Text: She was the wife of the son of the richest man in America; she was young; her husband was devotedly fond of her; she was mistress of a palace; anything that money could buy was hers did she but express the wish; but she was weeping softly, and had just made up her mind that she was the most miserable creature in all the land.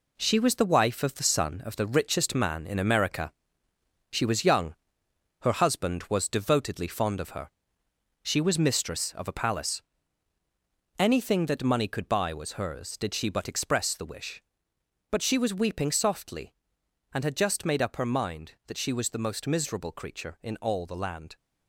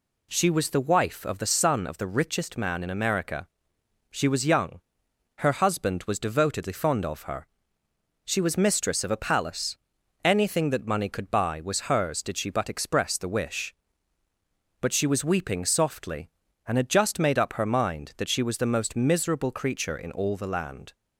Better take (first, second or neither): second